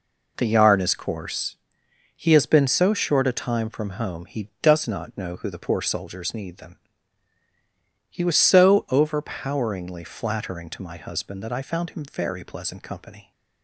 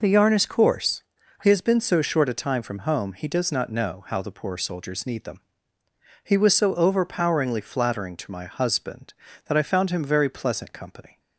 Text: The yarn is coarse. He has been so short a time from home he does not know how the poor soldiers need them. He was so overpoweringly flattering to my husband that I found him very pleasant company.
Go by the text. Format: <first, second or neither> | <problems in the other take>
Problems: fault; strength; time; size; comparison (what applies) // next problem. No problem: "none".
second | says "who" for "how"; at 5.3 s